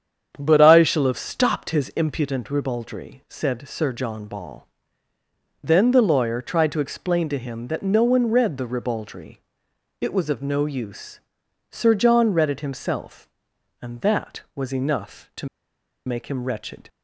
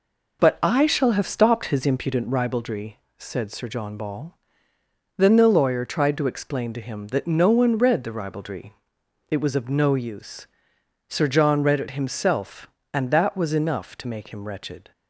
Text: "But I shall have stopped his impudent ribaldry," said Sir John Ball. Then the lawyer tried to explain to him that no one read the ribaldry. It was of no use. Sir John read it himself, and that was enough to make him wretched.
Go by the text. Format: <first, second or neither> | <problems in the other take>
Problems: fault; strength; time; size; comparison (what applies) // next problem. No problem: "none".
second | starts louder than the rest; strong; until 1.3 s; 8 dB // pauses between "to" and "make"; noticeable; at 15.4 s; 0.58 s long